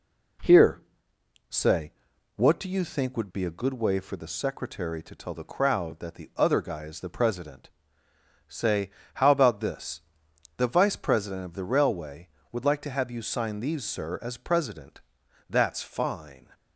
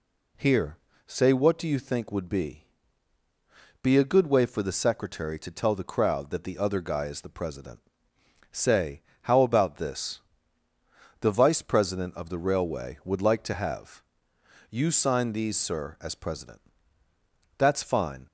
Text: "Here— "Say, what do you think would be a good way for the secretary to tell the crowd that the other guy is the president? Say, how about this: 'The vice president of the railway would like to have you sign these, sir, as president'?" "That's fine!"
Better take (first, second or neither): first